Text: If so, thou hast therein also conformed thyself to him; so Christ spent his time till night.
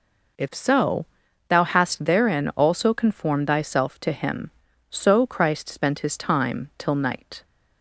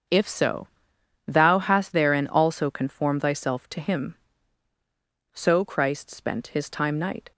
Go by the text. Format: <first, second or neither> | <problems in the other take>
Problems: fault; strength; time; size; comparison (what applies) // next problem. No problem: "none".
first | starts louder than the rest; until 1.6 s; 6.5 dB // skips "till"; at 6.9 s